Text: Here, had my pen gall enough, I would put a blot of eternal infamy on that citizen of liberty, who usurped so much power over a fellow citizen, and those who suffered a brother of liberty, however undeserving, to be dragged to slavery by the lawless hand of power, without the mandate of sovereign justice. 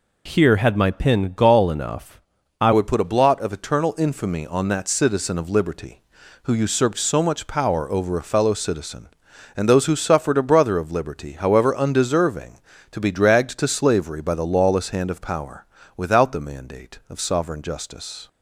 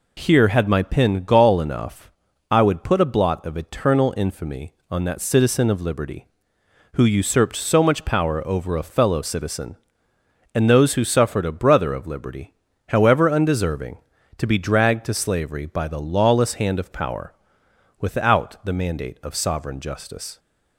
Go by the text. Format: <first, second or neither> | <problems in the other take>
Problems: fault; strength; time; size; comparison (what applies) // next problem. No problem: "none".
second | changes voice at "would"; from 2.7 s on; 15.5 s long